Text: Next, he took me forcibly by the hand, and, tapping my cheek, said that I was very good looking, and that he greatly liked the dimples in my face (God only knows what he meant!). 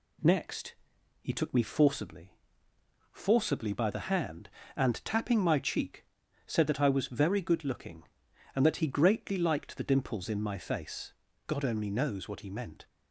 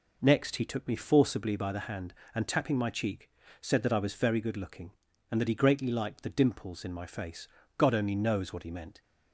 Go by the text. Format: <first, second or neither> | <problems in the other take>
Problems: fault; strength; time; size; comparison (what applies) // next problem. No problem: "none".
second | says "forcibly" twice; at 3.1 s